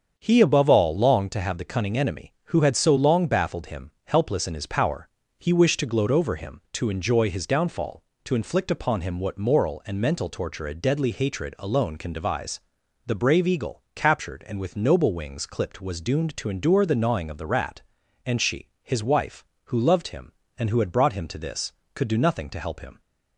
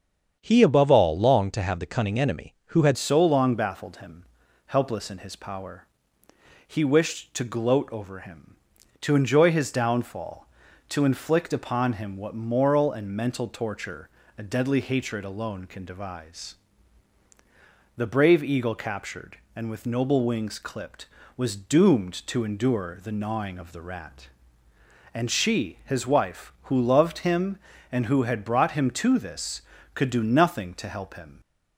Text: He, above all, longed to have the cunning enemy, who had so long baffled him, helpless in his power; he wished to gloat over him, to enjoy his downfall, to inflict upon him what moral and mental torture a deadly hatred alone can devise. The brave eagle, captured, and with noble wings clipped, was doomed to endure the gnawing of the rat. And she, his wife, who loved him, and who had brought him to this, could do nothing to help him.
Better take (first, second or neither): first